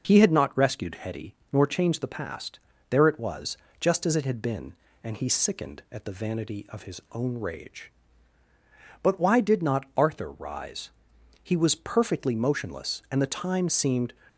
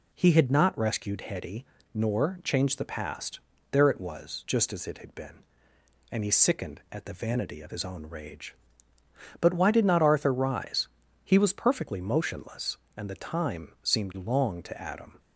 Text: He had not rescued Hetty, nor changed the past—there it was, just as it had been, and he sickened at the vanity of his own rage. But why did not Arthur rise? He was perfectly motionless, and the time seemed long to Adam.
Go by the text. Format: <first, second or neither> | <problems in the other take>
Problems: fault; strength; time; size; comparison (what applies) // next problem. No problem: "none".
second | stops before "long to Adam"; at 14.2 s